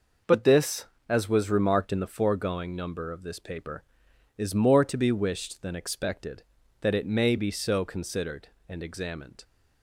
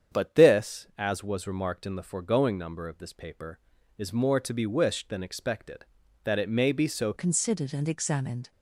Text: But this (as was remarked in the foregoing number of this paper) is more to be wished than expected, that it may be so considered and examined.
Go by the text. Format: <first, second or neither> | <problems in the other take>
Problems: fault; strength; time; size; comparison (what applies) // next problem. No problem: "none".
first | starts louder than the rest; strong; until 1.2 s; 8 dB // changes voice at "considered"; from 7.1 s on; 1.4 s long